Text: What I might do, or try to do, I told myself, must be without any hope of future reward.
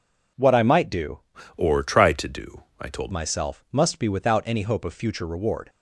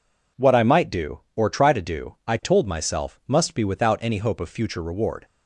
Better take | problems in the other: second | changes voice from "or" to "told"; from 1.5 to 3.1 s; 1.6 s long

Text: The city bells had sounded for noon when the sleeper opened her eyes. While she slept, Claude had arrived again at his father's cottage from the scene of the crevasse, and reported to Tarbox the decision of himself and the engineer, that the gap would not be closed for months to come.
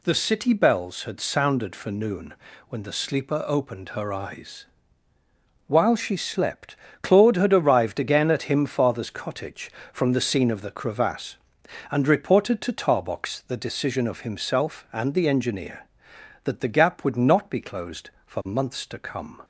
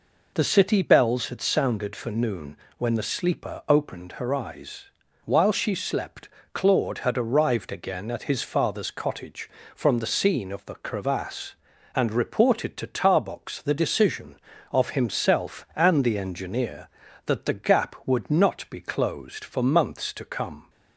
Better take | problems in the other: second | pauses between "noon" and "when"; slight; at 2.3 s; 0.36 s long; slight in the second // says "him" for "his"; at 8.4 s

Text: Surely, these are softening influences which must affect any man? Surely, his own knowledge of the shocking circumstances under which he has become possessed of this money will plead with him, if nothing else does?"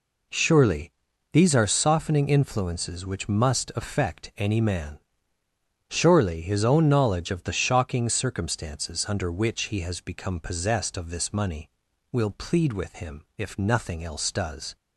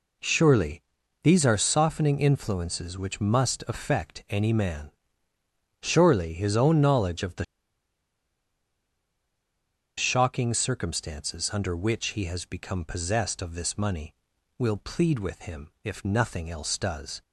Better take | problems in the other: first | pauses between "the" and "shocking"; strong; at 7.4 s; 2.5 s long

